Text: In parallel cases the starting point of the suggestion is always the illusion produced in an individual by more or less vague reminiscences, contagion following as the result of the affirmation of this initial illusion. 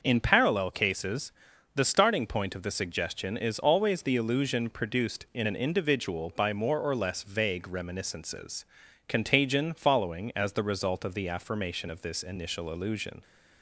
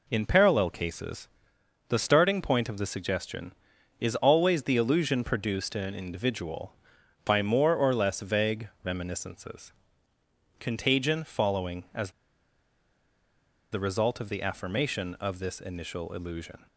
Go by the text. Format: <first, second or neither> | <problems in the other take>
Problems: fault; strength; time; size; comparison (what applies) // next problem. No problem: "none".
first | pauses between "cases" and "the"; noticeable; at 1.2 s; 0.62 s long; also in the first // pauses between "as" and "the"; strong; at 12.1 s; 1.6 s long